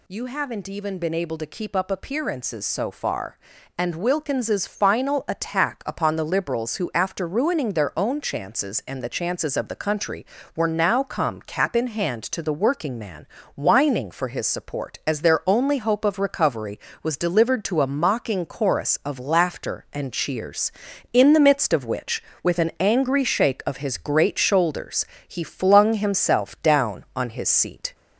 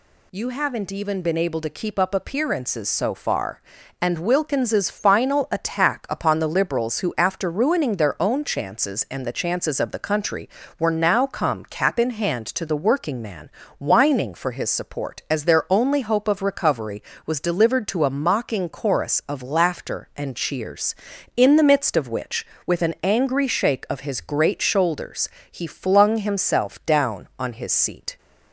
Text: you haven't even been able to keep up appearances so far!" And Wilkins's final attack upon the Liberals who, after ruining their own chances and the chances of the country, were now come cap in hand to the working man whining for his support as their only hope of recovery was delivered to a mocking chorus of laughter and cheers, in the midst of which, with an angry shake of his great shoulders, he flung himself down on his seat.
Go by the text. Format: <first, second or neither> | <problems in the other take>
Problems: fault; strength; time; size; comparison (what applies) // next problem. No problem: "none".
second | gets louder; slight; throughout; 2 dB // pauses between "man" and "whining"; slight; at 13.2 s; 0.28 s long; slight in the second